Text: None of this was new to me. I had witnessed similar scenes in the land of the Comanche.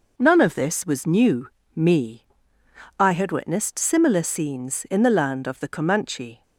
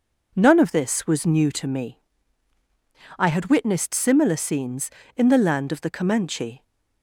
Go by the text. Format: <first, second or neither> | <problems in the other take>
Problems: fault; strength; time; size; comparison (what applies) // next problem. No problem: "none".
second | skips "to"; at 1.6 s